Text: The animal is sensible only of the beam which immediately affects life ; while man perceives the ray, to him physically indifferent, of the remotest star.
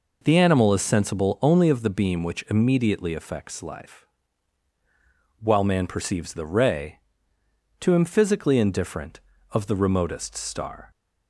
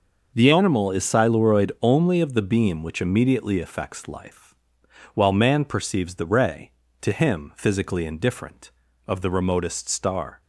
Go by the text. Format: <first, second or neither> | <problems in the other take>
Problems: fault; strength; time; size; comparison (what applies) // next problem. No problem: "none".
first | says "siluroid" for "sensible"; at 1.0 s